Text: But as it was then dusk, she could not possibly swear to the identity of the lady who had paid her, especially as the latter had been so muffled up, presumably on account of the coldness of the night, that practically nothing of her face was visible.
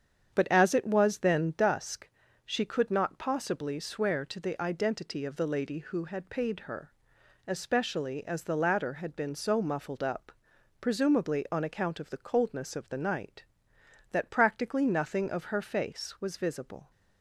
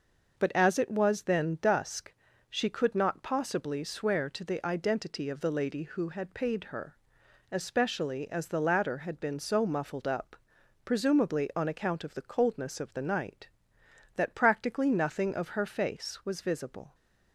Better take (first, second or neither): second